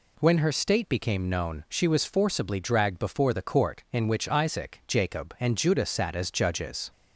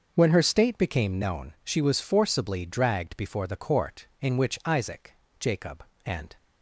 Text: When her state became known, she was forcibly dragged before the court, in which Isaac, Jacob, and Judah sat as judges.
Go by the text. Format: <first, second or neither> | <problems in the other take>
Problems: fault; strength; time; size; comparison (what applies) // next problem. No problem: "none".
first | stops before "Judah sat as judges"; at 6.3 s